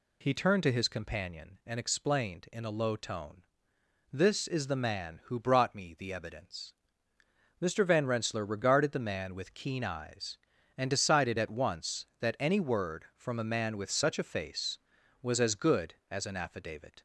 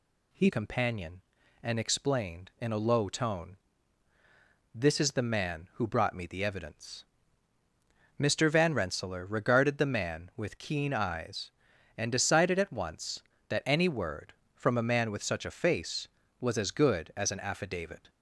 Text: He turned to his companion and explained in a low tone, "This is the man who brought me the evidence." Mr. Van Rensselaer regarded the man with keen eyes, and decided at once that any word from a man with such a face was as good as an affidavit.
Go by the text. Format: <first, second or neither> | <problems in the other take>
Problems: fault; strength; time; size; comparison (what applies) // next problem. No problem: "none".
first | skips "turned to his"; at 0.4 s